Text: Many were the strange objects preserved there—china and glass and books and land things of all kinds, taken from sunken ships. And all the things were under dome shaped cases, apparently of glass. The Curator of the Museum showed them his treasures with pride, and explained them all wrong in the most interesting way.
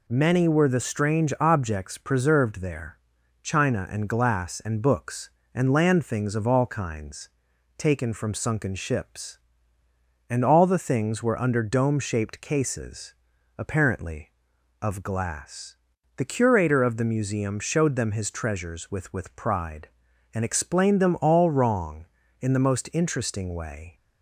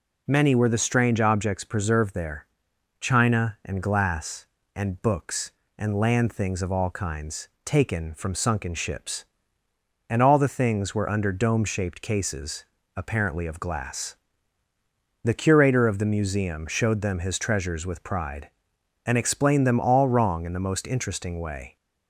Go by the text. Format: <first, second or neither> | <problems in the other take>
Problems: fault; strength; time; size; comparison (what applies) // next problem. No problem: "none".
second | says "with" twice; at 19.1 s